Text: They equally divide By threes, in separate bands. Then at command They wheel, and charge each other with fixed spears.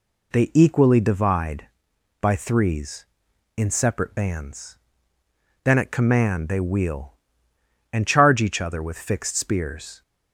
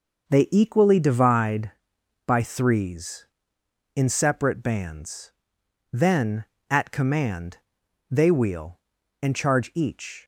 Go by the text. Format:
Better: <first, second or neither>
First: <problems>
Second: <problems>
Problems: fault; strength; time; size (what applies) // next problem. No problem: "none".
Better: first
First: none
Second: pauses between "command" and "They"; noticeable; at 7.5 s; 0.52 s long // stops before "other with fixed spears"; at 10.2 s